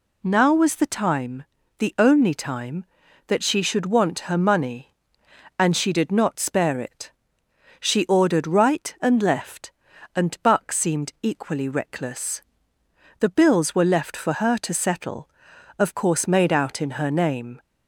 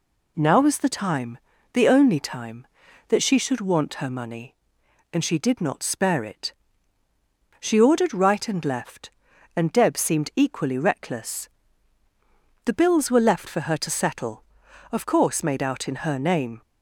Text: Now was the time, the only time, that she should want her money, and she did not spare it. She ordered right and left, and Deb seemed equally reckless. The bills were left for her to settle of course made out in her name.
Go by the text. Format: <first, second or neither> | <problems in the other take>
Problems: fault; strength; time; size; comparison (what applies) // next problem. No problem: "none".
second | says "Buck" for "Deb"; at 10.4 s